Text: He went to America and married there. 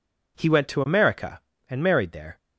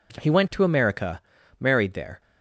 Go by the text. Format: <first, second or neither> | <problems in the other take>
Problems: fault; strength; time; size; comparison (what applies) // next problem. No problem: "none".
first | skips "and"; at 1.3 s